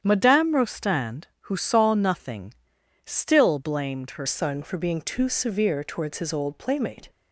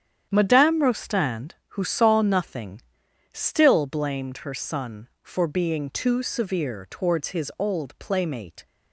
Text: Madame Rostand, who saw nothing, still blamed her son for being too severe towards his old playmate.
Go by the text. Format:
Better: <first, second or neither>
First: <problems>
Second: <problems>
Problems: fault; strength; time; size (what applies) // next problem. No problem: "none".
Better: second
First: starts louder than the rest; strong; until 1.0 s; 9 dB // changes voice at "son"; from 4.2 s on; 2.8 s long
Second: starts louder than the rest; strong; until 1.3 s; 9 dB